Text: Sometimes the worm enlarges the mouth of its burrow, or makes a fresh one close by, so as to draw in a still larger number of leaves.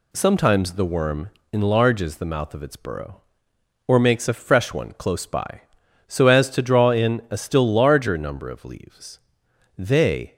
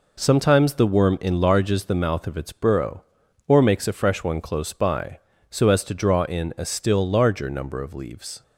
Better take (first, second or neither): second